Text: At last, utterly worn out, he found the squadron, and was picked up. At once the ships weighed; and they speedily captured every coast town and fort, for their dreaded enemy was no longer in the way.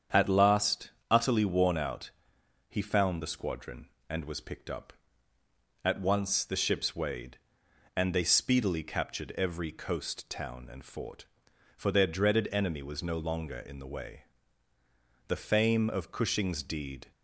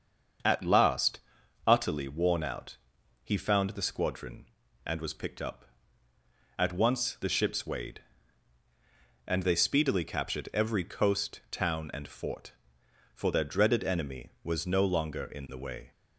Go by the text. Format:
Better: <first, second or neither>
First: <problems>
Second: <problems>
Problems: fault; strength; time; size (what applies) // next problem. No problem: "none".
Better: second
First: starts louder than the rest; strong; until 1.3 s; 8 dB // goes on to say "The fame of Cushing's deed"; strong; from 15.2 s on; 1.8 s long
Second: starts louder than the rest; until 1.9 s; 7 dB